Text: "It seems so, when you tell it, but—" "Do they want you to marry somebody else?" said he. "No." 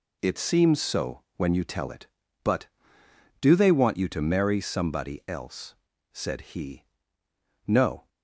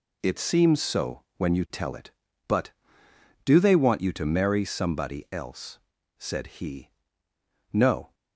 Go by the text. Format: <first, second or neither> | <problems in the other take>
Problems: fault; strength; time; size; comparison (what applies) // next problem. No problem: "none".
neither | none